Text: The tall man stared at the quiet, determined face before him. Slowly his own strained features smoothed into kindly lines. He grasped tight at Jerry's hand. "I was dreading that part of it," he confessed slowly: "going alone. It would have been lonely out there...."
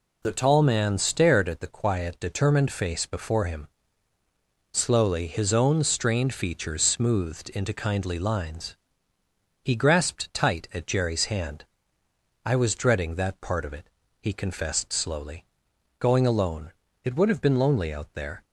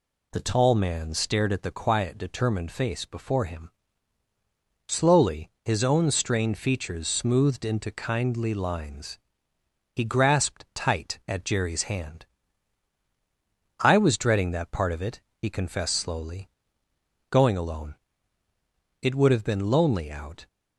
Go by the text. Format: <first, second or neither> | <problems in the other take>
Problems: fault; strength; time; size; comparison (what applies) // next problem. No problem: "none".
first | stops before "there"; at 20.4 s